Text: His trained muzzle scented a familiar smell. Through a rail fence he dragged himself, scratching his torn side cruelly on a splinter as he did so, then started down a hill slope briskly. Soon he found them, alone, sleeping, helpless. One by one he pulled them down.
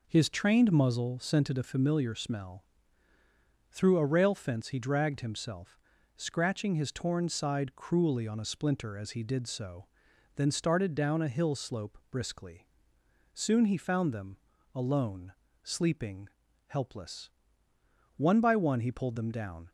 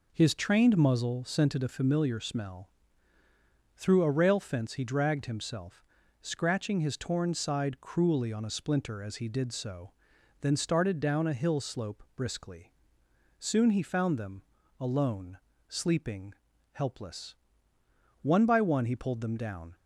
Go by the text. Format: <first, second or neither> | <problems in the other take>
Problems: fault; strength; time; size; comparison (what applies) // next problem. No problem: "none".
neither | none